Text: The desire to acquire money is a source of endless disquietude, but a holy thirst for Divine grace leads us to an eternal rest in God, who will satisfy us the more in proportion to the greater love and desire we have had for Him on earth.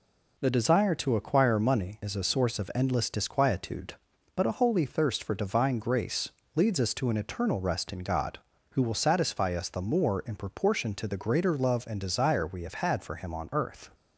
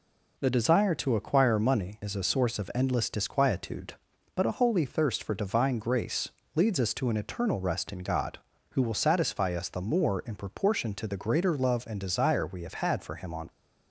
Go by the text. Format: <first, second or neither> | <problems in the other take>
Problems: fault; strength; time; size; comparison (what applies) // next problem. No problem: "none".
first | pauses between "grace" and "leads"; slight; at 6.2 s; 0.26 s long; slight in the first // stops before "earth"; at 13.4 s